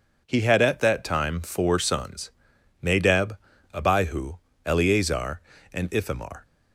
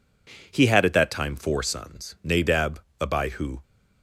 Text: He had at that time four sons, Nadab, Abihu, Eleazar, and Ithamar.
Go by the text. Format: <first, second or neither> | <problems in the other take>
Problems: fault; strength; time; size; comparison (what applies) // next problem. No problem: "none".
first | stops before "Eleazar and Ithamar"; at 3.6 s